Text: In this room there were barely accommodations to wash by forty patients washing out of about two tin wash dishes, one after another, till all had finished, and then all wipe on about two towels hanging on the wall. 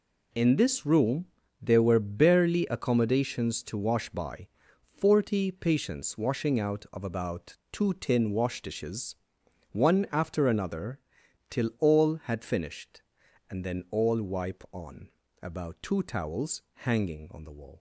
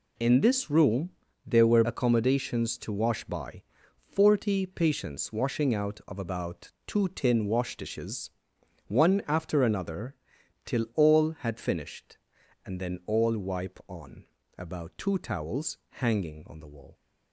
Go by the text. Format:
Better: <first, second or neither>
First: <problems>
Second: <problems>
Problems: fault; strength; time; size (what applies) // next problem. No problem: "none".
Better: first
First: pauses between "room" and "there"; slight; at 1.2 s; 0.36 s long // pauses between "by" and "forty"; noticeable; at 4.4 s; 0.50 s long // pauses between "about" and "two"; slight; at 7.5 s; 0.16 s long // pauses between "on" and "about"; slight; at 15.0 s; 0.34 s long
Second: pauses between "room" and "there"; slight; at 1.0 s; 0.36 s long // skips "barely"; at 1.8 s // pauses between "by" and "forty"; noticeable; at 3.6 s; 0.50 s long // pauses between "about" and "two"; slight; at 6.7 s; 0.16 s long // pauses between "on" and "about"; slight; at 14.2 s; 0.34 s long